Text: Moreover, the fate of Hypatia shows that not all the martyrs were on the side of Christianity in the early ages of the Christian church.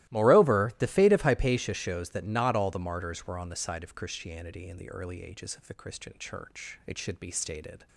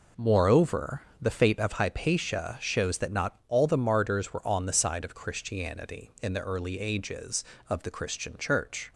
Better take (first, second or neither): second